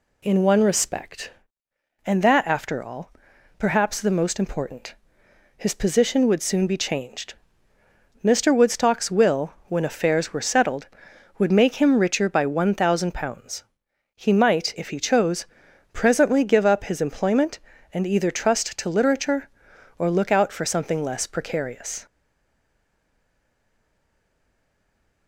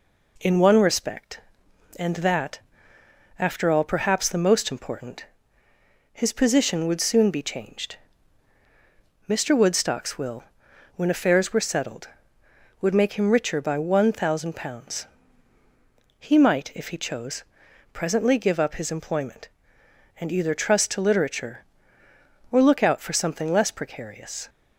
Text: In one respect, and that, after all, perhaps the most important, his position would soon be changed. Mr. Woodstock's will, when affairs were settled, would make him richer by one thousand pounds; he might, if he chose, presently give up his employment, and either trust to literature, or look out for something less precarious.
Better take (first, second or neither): second